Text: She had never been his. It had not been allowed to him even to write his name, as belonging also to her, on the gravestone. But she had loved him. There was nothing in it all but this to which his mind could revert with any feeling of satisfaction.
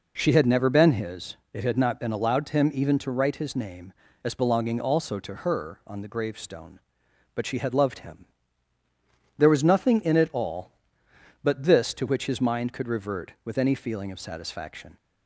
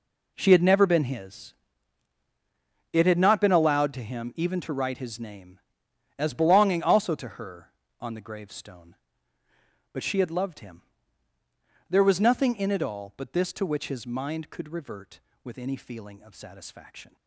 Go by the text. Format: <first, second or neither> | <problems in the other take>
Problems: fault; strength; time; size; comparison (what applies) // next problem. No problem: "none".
first | gets quieter; strong; throughout; 13.5 dB